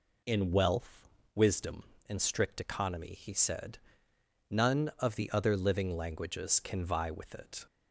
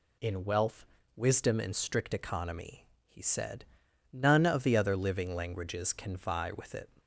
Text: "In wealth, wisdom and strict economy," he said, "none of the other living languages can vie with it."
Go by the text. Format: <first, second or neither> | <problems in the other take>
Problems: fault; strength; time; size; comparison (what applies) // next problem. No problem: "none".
neither | none